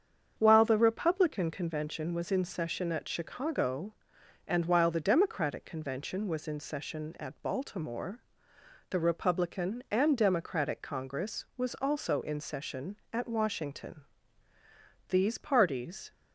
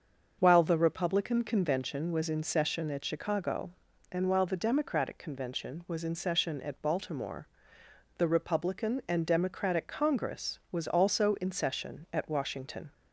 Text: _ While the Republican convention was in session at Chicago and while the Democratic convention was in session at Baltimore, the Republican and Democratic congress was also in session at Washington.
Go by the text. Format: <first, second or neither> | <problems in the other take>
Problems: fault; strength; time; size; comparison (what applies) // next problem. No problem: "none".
second | starts louder than the rest; strong; until 1.3 s; 7.5 dB; also in the second // goes on to say "These parties"; noticeable; from 15.0 s on; 1.0 s long